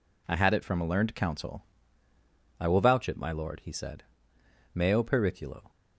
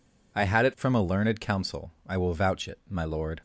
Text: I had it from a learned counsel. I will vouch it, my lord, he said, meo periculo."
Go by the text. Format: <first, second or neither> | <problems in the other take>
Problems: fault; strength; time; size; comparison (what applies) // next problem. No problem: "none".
first | stops before "he said meo periculo"; at 3.3 s